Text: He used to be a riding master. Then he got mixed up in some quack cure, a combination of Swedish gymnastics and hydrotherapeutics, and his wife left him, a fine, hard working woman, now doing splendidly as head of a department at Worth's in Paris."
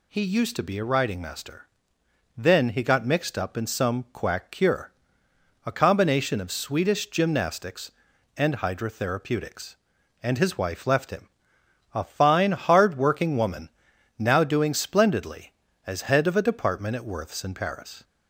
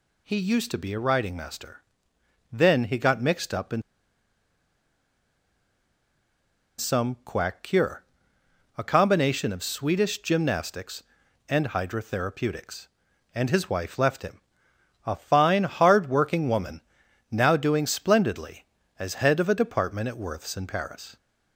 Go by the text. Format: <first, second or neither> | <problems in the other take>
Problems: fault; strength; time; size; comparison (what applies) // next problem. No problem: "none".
first | pauses between "in" and "some"; strong; at 3.8 s; 2.9 s long